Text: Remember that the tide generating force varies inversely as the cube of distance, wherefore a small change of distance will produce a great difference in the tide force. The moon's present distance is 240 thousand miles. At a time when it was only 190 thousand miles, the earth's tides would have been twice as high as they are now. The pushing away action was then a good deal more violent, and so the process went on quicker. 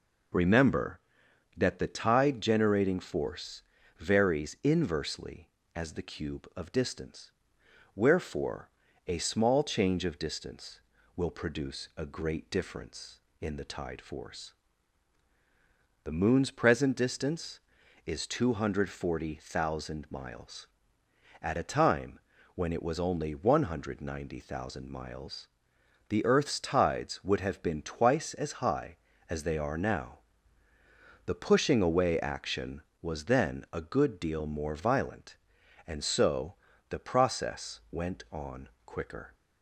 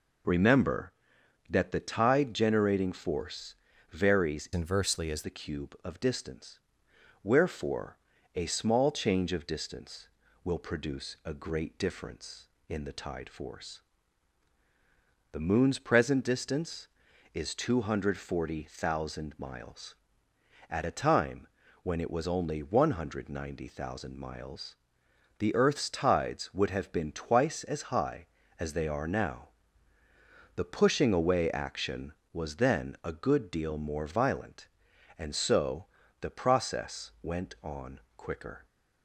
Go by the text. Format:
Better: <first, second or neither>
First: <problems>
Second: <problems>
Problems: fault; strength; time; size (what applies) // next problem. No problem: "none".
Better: first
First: pauses between "force" and "varies"; at 3.6 s; 0.38 s long // pauses between "wherefore" and "a"; at 8.6 s; 0.40 s long // pauses between "time" and "when"; at 22.1 s; 0.38 s long // pauses between "so" and "the"; slight; at 36.5 s; 0.34 s long // pauses between "on" and "quicker"; slight; at 38.6 s; 0.16 s long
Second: pauses between "force" and "varies"; at 3.5 s; 0.38 s long // changes voice from "inversely" to "as"; from 4.5 to 5.2 s; 0.7 s long // pauses between "wherefore" and "a"; at 7.9 s; 0.40 s long // pauses between "time" and "when"; at 21.4 s; 0.38 s long // pauses between "so" and "the"; slight; at 35.8 s; 0.34 s long // pauses between "on" and "quicker"; slight; at 38.0 s; 0.16 s long